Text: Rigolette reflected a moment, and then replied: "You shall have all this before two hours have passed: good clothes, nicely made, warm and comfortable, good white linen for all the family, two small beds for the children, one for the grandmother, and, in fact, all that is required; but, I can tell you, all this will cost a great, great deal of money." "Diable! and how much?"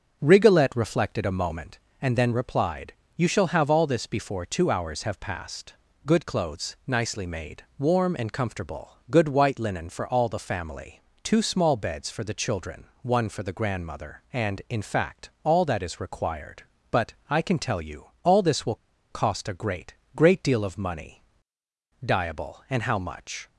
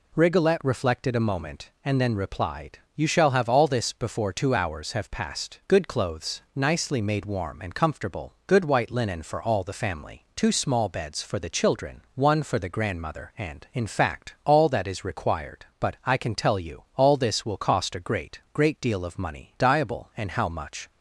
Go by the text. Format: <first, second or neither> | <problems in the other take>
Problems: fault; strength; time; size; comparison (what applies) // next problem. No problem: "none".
second | starts louder than the rest; until 1.2 s; 6.5 dB // pauses between "will" and "cost"; at 18.7 s; 0.36 s long